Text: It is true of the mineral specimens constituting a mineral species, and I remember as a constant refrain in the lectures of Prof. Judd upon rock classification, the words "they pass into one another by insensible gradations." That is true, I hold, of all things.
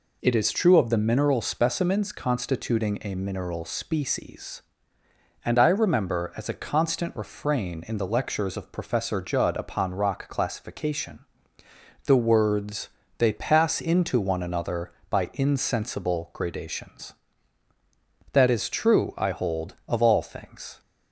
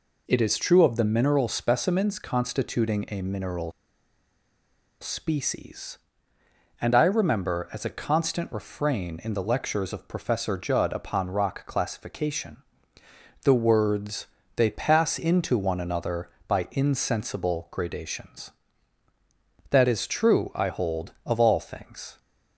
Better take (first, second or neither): first